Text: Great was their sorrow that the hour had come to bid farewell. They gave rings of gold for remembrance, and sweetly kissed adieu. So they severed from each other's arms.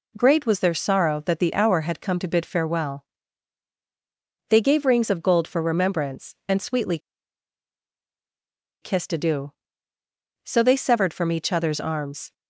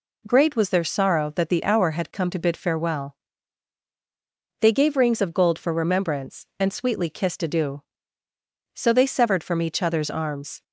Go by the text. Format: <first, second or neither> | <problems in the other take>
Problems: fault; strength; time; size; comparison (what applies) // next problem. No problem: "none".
second | pauses between "sweetly" and "kissed"; strong; at 6.9 s; 1.8 s long